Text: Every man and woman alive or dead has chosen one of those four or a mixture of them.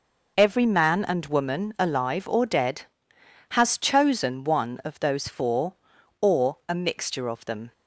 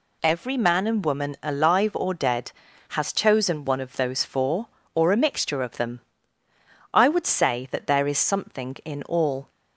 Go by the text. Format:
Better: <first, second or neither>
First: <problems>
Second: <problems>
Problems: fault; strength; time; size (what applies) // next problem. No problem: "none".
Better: first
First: none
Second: goes on to say "I would say that there is something in all"; strong; from 6.9 s on; 2.5 s long